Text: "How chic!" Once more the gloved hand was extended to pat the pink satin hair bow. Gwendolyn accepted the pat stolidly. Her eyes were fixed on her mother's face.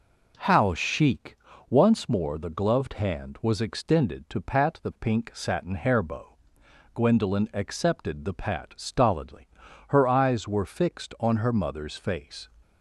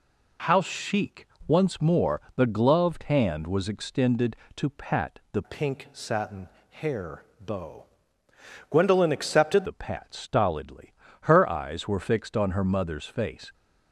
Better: first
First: none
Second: pauses between "more" and "the"; slight; at 2.1 s; 0.16 s long // changes voice from "pink" to "accepted"; from 5.4 to 9.6 s; 4.2 s long // pauses between "satin" and "hair"; slight; at 6.4 s; 0.22 s long // pauses between "hair" and "bow"; slight; at 7.2 s; 0.18 s long

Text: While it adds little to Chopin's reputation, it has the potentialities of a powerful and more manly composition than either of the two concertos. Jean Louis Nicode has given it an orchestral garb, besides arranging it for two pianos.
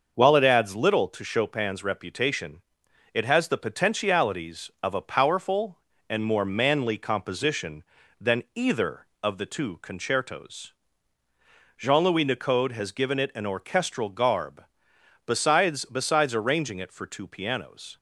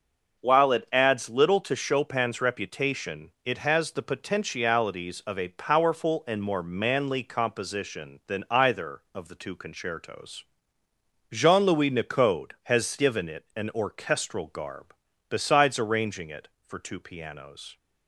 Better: second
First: starts louder than the rest; until 1.1 s; 6 dB // says "besides" twice; at 15.8 s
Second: none

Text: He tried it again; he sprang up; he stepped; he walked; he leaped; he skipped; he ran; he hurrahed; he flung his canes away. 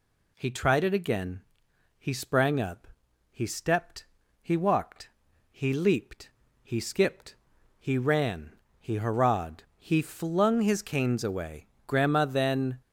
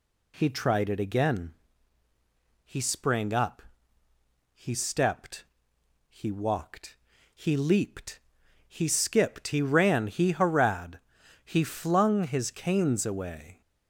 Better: second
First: goes on to say "Grandma then"; noticeable; from 11.8 s on; 0.94 s long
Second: none

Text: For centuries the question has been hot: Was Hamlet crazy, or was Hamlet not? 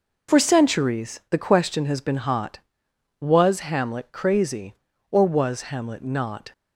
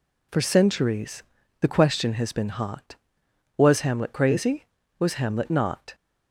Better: first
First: none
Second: pauses between "centuries" and "the"; slight; at 1.2 s; 0.36 s long // skips "or"; at 4.8 s

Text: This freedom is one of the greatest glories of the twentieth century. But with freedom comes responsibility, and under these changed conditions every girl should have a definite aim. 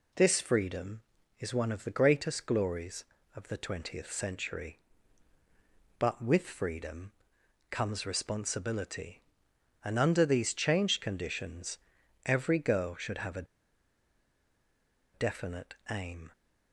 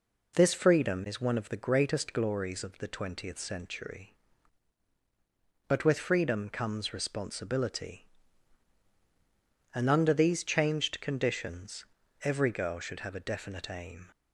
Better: second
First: pauses between "freedom" and "comes"; noticeable; at 7.1 s; 0.58 s long // pauses between "conditions" and "every"; noticeable; at 11.7 s; 0.48 s long // pauses between "a" and "definite"; strong; at 13.4 s; 1.6 s long // pauses between "definite" and "aim"; slight; at 15.7 s; 0.16 s long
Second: pauses between "conditions" and "every"; at 11.8 s; 0.40 s long

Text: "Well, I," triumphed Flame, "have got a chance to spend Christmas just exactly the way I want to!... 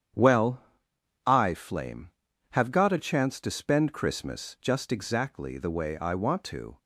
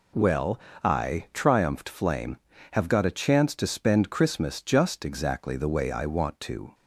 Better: second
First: starts louder than the rest; strong; until 1.8 s; 9 dB // skips "triumphed"; at 1.5 s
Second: none

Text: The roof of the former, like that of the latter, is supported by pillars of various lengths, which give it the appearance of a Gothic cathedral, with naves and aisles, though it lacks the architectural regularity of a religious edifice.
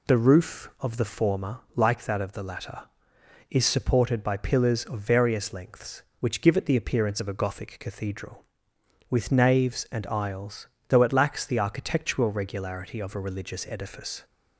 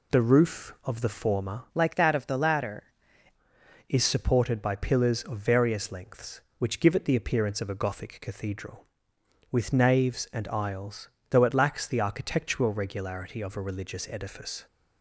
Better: first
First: none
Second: changes voice from "like" to "latter"; from 1.7 to 2.8 s; 1.1 s long

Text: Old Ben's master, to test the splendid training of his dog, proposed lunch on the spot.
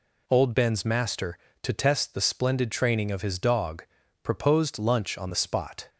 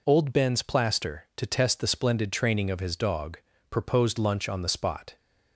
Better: first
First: none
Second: says "plaster" for "master"; at 0.6 s

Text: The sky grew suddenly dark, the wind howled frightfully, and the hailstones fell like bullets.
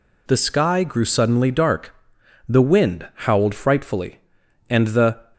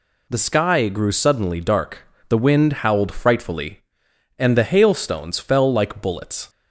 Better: second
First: pauses between "wind" and "howled"; slight; at 3.0 s; 0.18 s long // stops before "hailstones fell like bullets"; at 5.3 s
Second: none

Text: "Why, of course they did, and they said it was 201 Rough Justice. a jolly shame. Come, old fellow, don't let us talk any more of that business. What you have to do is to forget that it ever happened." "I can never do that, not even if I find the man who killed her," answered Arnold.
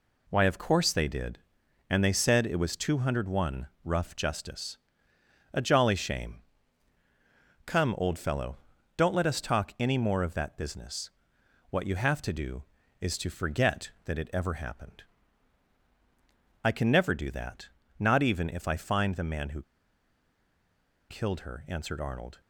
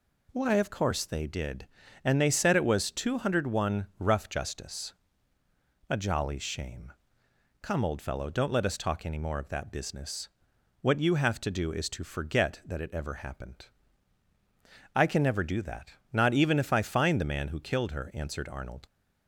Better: second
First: pauses between "who" and "killed"; strong; at 19.6 s; 1.4 s long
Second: none

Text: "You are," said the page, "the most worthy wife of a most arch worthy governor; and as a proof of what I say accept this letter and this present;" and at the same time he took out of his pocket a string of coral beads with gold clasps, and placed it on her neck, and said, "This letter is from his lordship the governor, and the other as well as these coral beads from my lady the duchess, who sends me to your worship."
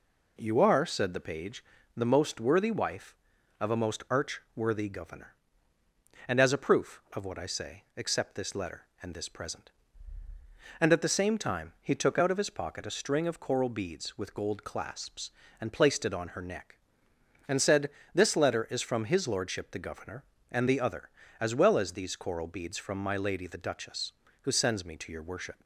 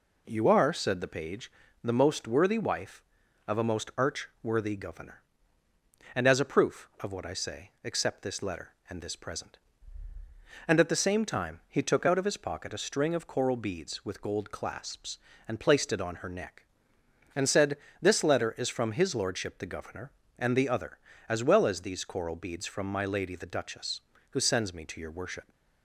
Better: neither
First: none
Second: none

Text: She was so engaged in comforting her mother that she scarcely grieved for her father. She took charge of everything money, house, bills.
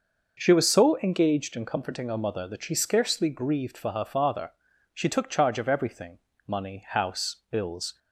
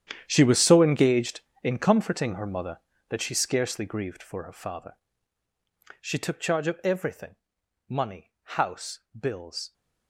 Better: first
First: pauses between "everything" and "money"; slight; at 6.1 s; 0.28 s long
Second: gets quieter; strong; throughout; 15 dB // pauses between "everything" and "money"; noticeable; at 7.3 s; 0.54 s long

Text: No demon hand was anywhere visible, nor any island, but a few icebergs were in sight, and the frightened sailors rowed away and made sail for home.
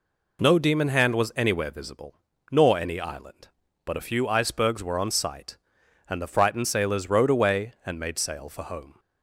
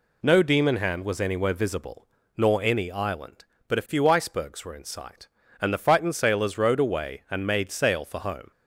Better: second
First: says "on" for "in"; at 4.9 s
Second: none

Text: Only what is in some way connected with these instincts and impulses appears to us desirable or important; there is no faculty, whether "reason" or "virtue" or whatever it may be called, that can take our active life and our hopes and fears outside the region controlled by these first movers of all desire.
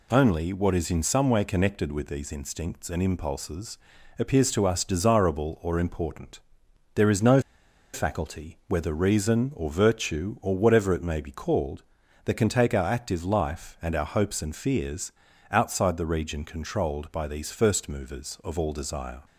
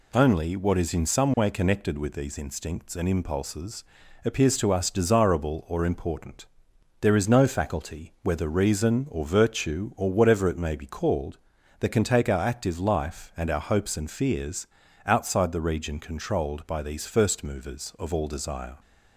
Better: second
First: pauses between "impulses" and "appears"; at 3.7 s; 0.44 s long // pauses between "no" and "faculty"; noticeable; at 7.3 s; 0.53 s long // pauses between "fears" and "outside"; at 15.1 s; 0.40 s long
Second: pauses between "impulses" and "appears"; at 3.8 s; 0.44 s long // pauses between "fears" and "outside"; at 14.6 s; 0.40 s long

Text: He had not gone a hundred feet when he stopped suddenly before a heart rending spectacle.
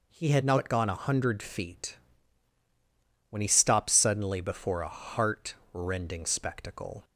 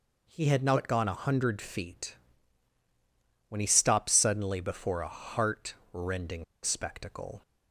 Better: first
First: pauses between "feet" and "when"; strong; at 1.9 s; 1.3 s long // pauses between "heart" and "rending"; slight; at 5.5 s; 0.18 s long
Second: pauses between "feet" and "when"; strong; at 2.1 s; 1.3 s long // pauses between "heart" and "rending"; slight; at 5.7 s; 0.18 s long // pauses between "rending" and "spectacle"; slight; at 6.4 s; 0.19 s long

